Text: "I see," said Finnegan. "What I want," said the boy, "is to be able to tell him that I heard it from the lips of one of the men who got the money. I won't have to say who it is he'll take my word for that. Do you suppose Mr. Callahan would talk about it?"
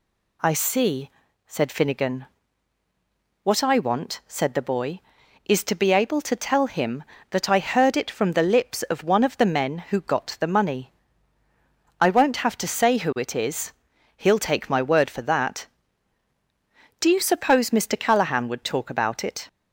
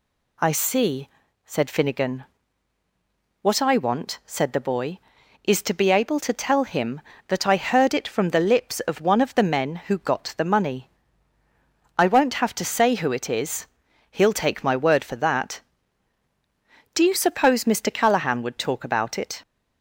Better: neither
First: pauses between "is" and "he'll"; noticeable; at 13.7 s; 0.46 s long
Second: pauses between "is" and "he'll"; noticeable; at 13.6 s; 0.46 s long

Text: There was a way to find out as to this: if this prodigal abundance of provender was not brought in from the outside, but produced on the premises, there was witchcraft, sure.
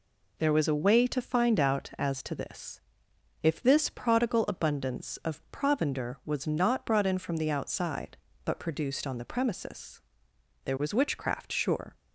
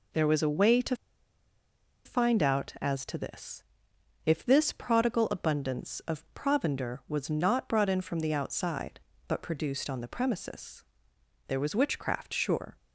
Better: first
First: none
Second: pauses between "to" and "find"; at 0.9 s; 1.0 s long

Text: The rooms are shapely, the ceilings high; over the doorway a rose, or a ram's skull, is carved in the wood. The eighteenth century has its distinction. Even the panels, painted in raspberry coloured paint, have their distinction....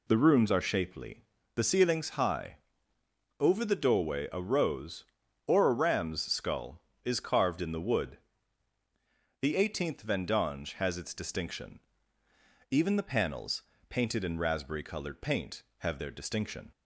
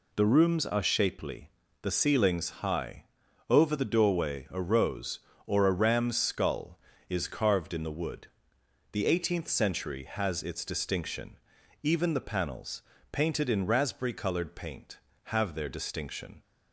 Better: second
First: says "vendange" for "century"; at 10.0 s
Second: none

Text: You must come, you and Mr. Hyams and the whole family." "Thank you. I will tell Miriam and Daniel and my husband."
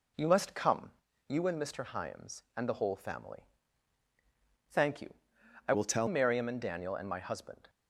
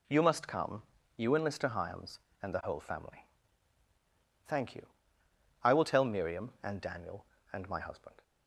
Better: second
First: changes voice from "will" to "tell"; from 5.7 to 6.0 s; 0.3 s long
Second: none

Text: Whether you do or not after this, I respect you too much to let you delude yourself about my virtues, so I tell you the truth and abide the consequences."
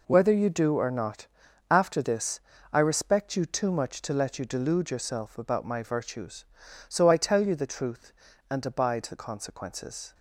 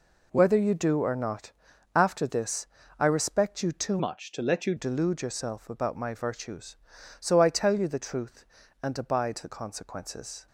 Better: first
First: pauses between "not" and "after"; at 1.2 s; 0.44 s long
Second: pauses between "not" and "after"; at 1.5 s; 0.44 s long // changes voice from "much" to "you"; from 3.9 to 4.7 s; 0.8 s long

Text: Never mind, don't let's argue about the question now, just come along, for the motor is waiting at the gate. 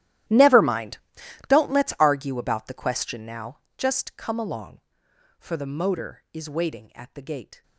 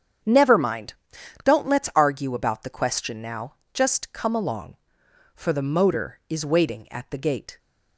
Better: second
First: gets quieter; strong; throughout; 21 dB // starts louder than the rest; strong; until 1.7 s; 14 dB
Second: starts louder than the rest; strong; until 1.7 s; 8 dB

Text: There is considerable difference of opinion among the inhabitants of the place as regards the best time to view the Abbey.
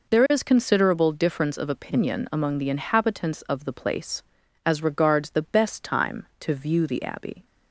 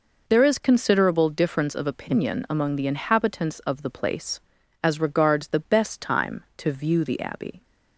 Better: neither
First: none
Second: none

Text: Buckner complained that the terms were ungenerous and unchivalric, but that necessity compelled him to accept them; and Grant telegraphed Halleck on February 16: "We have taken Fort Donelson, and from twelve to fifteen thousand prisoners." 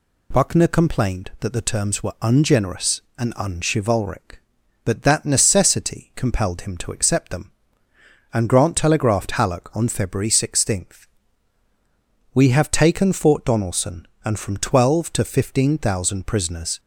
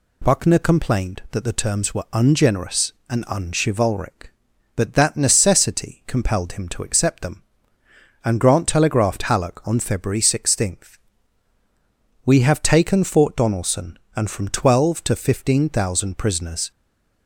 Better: first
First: none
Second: stays silent after the last word; slight; from 16.7 s on; 0.5 s long

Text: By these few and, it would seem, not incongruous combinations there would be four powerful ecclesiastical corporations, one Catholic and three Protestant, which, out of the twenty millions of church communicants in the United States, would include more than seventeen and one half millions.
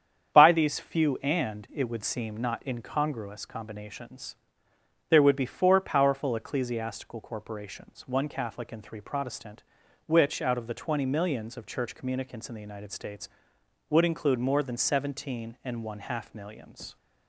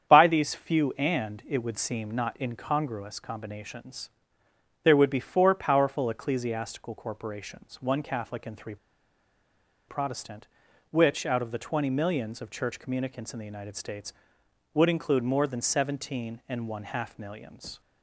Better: first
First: starts louder than the rest; strong; until 1.3 s; 8 dB // pauses between "combinations" and "there"; noticeable; at 4.3 s; 0.74 s long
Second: starts louder than the rest; strong; until 1.1 s; 8 dB // pauses between "combinations" and "there"; noticeable; at 4.0 s; 0.74 s long // pauses between "three" and "Protestant"; at 8.7 s; 1.1 s long

